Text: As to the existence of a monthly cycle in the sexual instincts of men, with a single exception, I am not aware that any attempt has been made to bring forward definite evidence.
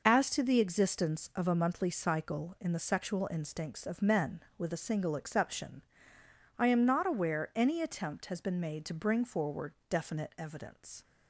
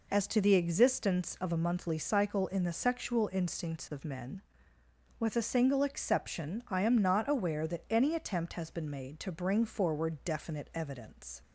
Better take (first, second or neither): second